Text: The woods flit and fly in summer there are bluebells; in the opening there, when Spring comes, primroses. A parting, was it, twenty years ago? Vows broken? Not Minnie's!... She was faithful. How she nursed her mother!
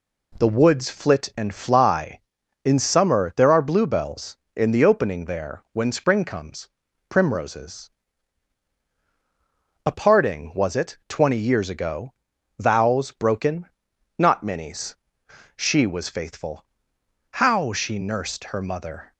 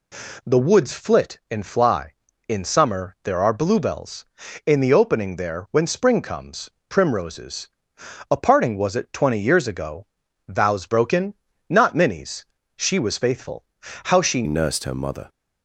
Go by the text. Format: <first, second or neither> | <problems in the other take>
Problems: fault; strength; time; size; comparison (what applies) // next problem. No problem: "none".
first | changes voice at "nursed"; from 14.4 s on; 0.8 s long